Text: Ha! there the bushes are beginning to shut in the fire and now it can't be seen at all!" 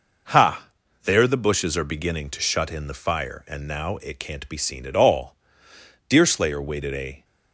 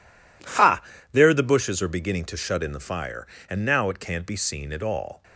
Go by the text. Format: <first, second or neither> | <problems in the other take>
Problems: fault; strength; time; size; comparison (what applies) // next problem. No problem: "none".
second | goes on to say "Deerslayer waited a"; noticeable; from 6.0 s on; 1.1 s long